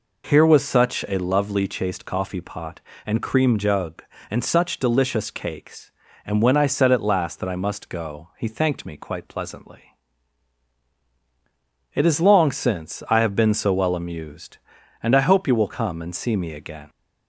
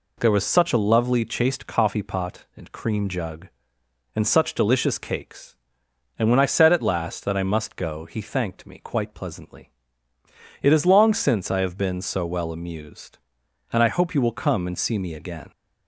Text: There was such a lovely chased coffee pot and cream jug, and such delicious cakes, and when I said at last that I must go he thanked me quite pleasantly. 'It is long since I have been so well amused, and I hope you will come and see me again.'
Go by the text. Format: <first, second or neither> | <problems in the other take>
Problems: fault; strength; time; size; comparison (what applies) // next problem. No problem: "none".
second | says "Here" for "There"; at 0.2 s